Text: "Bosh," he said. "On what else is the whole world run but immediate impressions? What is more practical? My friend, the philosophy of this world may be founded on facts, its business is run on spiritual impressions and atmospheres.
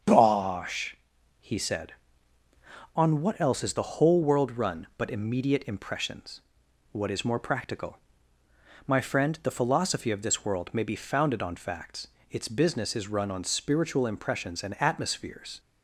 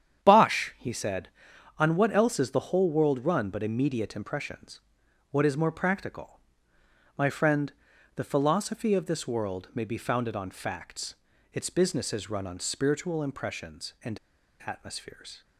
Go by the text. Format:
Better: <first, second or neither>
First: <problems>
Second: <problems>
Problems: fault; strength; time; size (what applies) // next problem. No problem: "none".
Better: first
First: starts louder than the rest; strong; until 1.4 s; 7.5 dB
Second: starts louder than the rest; strong; until 1.2 s; 9 dB // pauses between "and" and "atmospheres"; noticeable; at 14.1 s; 0.46 s long